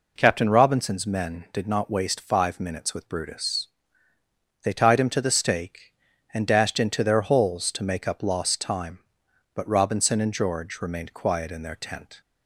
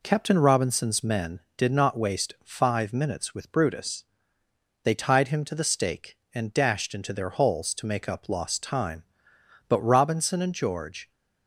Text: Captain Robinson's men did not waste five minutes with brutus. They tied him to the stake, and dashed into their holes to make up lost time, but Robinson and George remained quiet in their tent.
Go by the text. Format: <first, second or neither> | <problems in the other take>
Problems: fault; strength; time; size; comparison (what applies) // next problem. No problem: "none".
first | stops before "remained quiet in their tent"; at 11.1 s